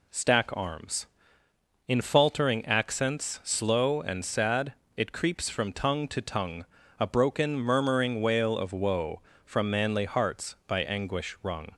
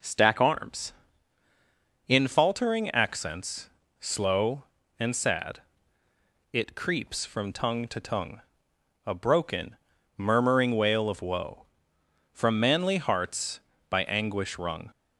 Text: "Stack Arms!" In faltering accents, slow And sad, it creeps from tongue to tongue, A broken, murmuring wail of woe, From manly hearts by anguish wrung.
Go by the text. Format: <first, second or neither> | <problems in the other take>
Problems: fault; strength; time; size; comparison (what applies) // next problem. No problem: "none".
neither | none